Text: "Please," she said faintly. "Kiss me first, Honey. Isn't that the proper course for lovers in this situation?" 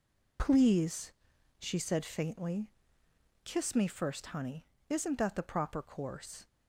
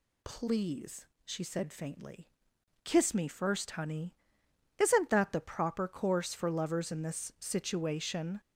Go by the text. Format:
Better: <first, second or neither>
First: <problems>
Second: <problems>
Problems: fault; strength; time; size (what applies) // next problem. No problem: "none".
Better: second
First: stops before "for lovers in this situation"; at 6.4 s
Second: none